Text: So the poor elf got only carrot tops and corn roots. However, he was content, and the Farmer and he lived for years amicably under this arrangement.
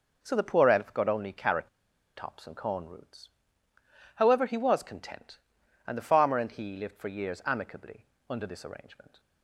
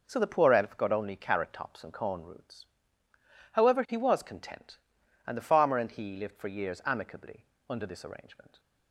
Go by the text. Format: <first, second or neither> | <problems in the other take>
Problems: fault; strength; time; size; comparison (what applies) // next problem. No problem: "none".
second | pauses between "carrot" and "tops"; noticeable; at 1.6 s; 0.47 s long // pauses between "amicably" and "under"; slight; at 8.0 s; 0.24 s long; slight in the second